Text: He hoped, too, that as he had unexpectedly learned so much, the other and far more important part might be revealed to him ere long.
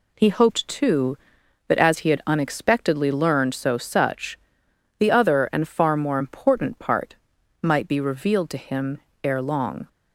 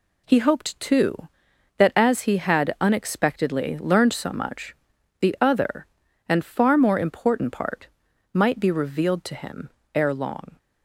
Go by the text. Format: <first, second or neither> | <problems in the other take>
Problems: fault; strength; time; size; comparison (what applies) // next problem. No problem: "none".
second | says "such" for "much"; at 3.7 s // pauses between "part" and "might"; noticeable; at 7.1 s; 0.46 s long; noticeable in the second // pauses between "him" and "ere"; slight; at 8.9 s; 0.24 s long; slight in the second